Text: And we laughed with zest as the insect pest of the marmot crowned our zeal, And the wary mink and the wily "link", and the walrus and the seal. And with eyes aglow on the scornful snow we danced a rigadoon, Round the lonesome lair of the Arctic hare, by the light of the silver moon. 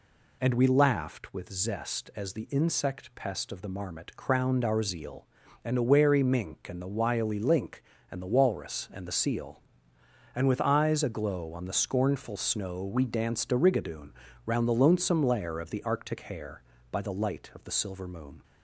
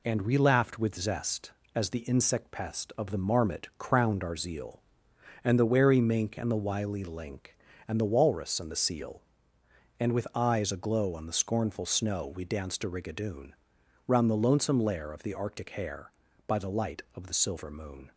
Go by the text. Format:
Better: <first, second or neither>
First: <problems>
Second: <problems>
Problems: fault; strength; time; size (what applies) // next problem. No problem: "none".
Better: neither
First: none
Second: none